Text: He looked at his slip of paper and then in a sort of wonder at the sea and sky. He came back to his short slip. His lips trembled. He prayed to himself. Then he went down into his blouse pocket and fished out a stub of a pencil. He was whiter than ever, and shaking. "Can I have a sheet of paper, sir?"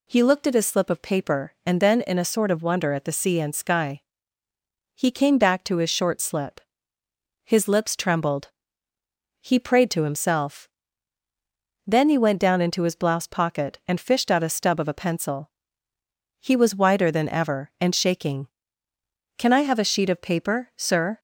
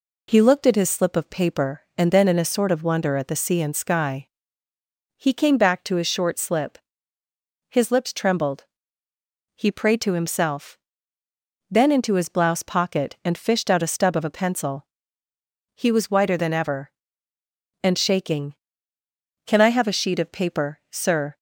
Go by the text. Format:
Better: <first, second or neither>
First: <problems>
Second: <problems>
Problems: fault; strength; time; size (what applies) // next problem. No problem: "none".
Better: first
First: none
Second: skips "he went down"; at 11.9 s